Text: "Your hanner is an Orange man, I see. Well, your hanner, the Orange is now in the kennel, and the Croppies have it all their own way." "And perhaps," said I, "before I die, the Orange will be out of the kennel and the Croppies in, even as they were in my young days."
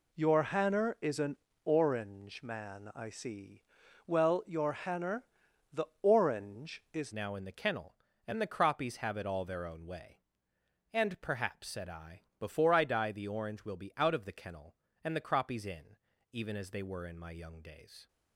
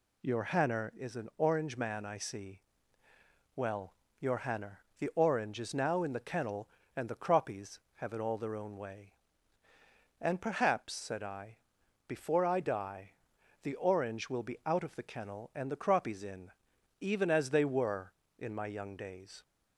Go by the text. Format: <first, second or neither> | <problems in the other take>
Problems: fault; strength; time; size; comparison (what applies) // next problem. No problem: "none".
second | pauses between "an" and "Orange"; slight; at 1.3 s; 0.26 s long // pauses between "the" and "Orange"; slight; at 5.8 s; 0.16 s long // changes voice at "now"; from 7.1 s on; 10.9 s long